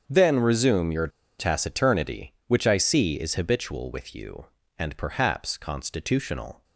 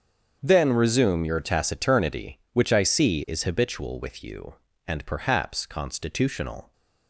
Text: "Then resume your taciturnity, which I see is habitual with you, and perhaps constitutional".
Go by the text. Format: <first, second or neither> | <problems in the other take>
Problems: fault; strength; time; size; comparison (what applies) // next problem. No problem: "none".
second | starts louder than the rest; strong; until 1.0 s; 7 dB; also in the second // pauses between "your" and "taciturnity"; slight; at 1.0 s; 0.30 s long